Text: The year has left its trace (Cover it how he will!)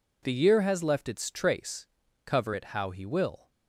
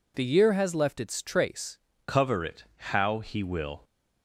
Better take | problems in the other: first | changes voice at "Cover"; from 2.0 s on; 1.8 s long

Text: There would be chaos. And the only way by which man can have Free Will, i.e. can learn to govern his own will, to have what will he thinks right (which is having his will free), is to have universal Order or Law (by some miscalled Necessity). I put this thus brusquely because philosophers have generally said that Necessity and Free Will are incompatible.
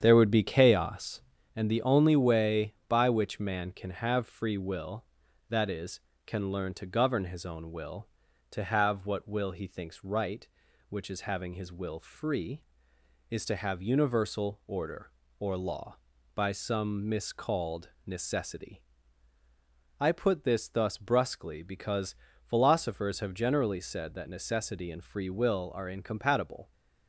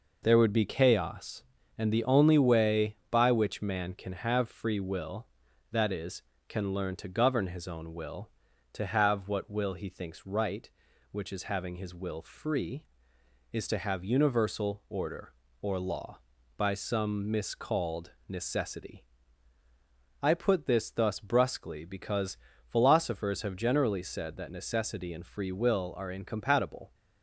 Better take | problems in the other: second | starts louder than the rest; strong; until 1.5 s; 8.5 dB // pauses between "because" and "philosophers"; slight; at 22.1 s; 0.28 s long; slight in the second

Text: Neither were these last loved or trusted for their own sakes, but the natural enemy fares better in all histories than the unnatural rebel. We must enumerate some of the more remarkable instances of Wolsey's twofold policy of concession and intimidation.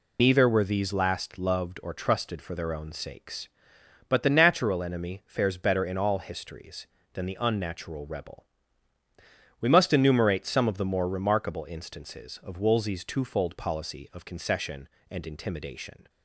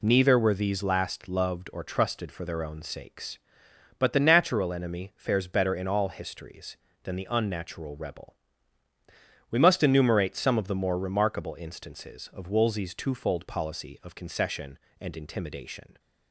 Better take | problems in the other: second | loses the start of "Neither"; at 0.1 s; 70 ms

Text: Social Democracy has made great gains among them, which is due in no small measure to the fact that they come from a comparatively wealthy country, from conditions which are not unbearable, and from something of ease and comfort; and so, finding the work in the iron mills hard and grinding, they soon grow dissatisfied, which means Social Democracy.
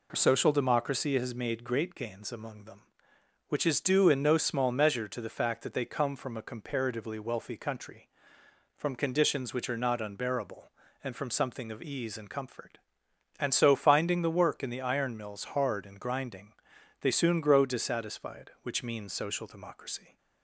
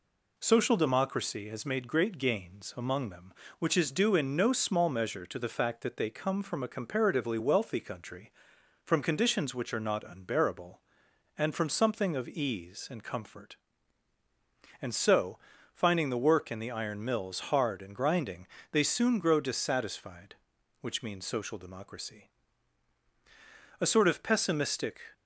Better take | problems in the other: first | goes on to say "A sort of pessimistic"; noticeable; from 23.7 s on; 1.2 s long

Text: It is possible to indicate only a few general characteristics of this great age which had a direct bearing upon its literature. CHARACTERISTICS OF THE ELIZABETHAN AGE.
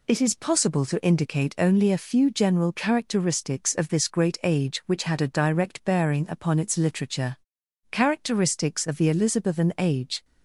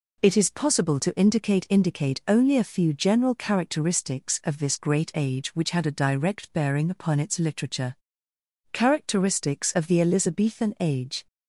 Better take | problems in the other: first | says "indicate" twice; at 1.6 s

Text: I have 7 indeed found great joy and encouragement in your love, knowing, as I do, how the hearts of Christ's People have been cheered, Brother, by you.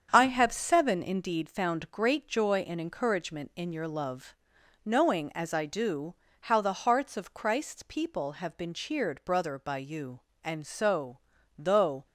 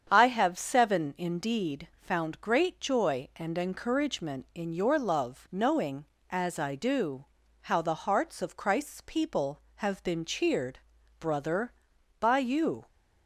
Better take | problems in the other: second | starts louder than the rest; strong; until 1.1 s; 7.5 dB; strong in the second // goes on to say "And so though"; from 10.4 s on; 1.6 s long

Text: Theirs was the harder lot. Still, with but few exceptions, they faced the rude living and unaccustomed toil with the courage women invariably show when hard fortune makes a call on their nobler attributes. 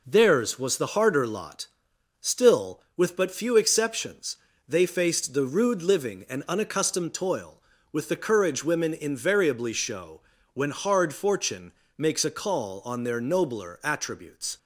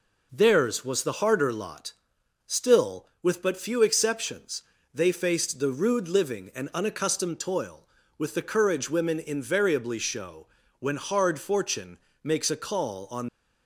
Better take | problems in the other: first | pauses between "show" and "when"; slight; at 10.4 s; 0.32 s long; slight in the first // pauses between "fortune" and "makes"; slight; at 11.9 s; 0.24 s long; slight in the first // stops before "their nobler attributes"; at 13.2 s

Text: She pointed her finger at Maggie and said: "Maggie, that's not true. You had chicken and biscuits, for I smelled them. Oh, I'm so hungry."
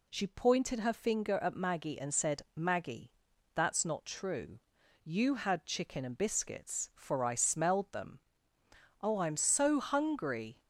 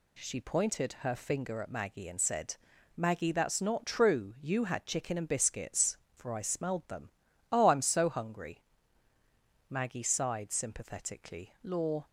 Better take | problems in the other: first | goes on to say "Maggie sighed sympathetically Law"; strong; from 9.6 s on; 2.3 s long

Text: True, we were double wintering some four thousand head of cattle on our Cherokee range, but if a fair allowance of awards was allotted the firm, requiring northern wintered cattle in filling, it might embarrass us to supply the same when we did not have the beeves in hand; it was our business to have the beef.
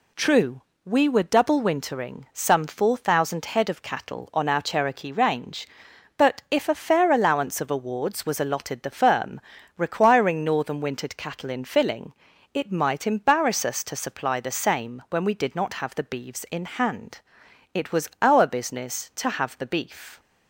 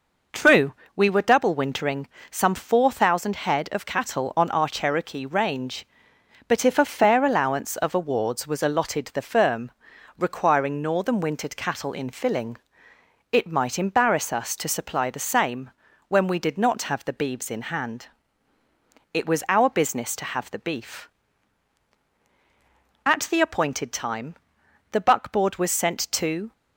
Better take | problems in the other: first | pauses between "wintering" and "some"; slight; at 2.0 s; 0.22 s long // pauses between "same" and "when"; at 15.6 s; 0.38 s long // goes on to say "At the appointed time the buckboard was sent to"; strong; from 23.0 s on; 3.4 s long

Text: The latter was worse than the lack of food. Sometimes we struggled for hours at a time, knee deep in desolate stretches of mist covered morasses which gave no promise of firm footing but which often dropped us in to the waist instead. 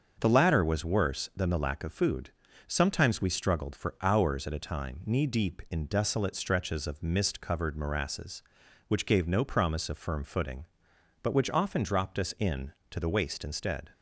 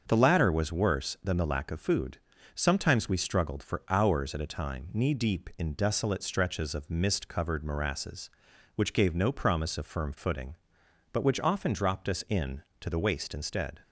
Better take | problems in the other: neither | starts louder than the rest; the same in both

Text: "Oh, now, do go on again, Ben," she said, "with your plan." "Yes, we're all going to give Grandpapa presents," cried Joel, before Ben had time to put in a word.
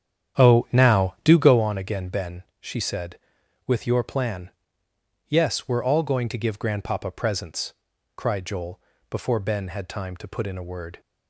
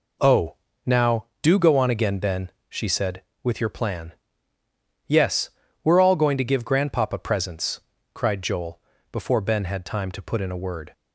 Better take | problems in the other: second | starts louder than the rest; strong; until 1.6 s; 9 dB

